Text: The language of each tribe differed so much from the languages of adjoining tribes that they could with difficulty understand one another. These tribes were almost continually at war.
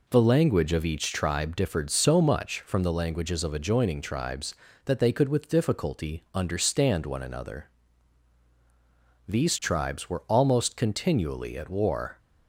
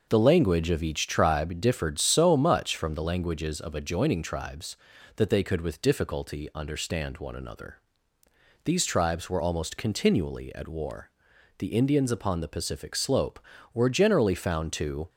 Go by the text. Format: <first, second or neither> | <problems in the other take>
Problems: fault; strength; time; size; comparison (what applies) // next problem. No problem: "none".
first | goes on to say "The Indians upon the Pacific slope were generally found to"; strong; from 11.5 s on; 3.5 s long